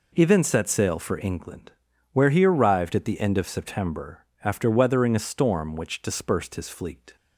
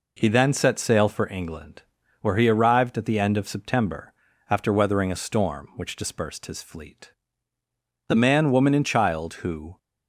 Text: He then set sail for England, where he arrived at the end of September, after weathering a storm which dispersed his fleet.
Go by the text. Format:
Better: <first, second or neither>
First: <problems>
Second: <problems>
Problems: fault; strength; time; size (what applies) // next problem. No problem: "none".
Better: first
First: none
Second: goes on to say "The man woman and child who"; strong; from 8.0 s on; 1.7 s long